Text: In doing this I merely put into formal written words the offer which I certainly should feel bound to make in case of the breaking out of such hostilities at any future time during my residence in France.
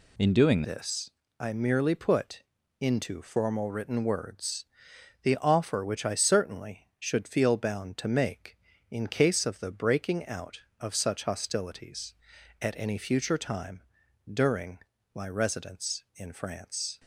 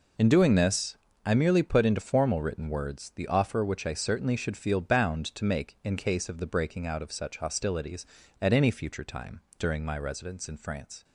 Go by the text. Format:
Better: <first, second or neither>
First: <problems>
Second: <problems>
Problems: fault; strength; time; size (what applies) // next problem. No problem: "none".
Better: second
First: changes voice at "this"; from 0.6 s on; 16.3 s long // pauses between "this" and "I"; slight; at 1.0 s; 0.30 s long // pauses between "put" and "into"; slight; at 2.4 s; 0.36 s long // pauses between "words" and "the"; noticeable; at 4.6 s; 0.58 s long // pauses between "time" and "during"; noticeable; at 13.8 s; 0.50 s long // pauses between "during" and "my"; slight; at 14.7 s; 0.36 s long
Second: pauses between "this" and "I"; slight; at 0.9 s; 0.28 s long // pauses between "time" and "during"; slight; at 9.3 s; 0.18 s long